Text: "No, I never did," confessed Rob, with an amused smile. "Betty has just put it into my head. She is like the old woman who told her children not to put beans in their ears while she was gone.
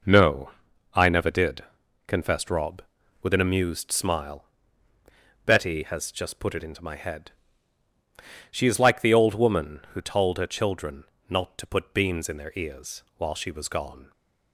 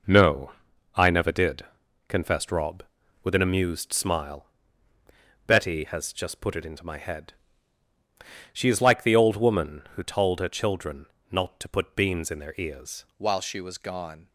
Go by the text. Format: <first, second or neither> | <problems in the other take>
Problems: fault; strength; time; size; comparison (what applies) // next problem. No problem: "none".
first | pauses between "children" and "not"; slight; at 11.0 s; 0.26 s long; slight in the first // changes voice at "while"; from 13.1 s on; 1.1 s long